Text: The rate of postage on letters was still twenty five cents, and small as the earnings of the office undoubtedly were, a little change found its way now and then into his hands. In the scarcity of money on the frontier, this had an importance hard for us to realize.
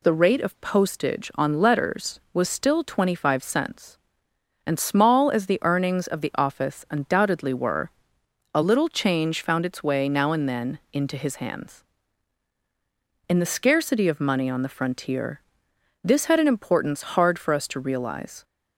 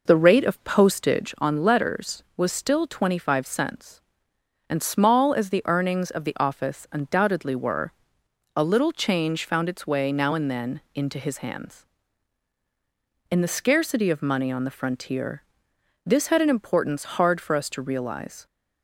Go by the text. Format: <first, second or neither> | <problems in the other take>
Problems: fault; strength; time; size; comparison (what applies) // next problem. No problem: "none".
first | starts louder than the rest; noticeable; until 1.4 s; 4.5 dB